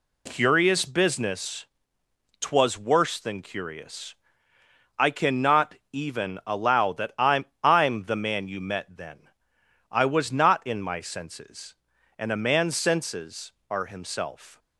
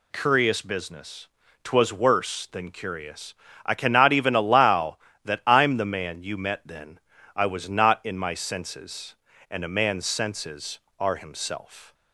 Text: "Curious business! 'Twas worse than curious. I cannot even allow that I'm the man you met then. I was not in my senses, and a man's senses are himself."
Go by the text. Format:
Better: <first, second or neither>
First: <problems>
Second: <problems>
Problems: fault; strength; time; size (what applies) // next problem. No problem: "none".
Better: second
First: pauses between "cannot" and "even"; slight; at 5.7 s; 0.16 s long // says "I'm" twice; at 7.6 s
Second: none